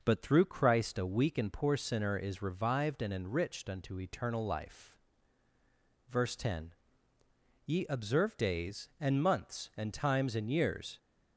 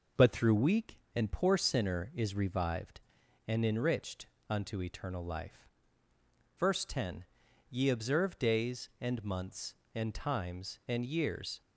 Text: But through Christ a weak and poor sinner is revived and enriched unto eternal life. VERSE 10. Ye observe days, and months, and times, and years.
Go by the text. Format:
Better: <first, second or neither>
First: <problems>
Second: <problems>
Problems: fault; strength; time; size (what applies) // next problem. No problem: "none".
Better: first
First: none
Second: skips "Christ a"; at 0.5 s // pauses between "enriched" and "unto"; slight; at 4.2 s; 0.22 s long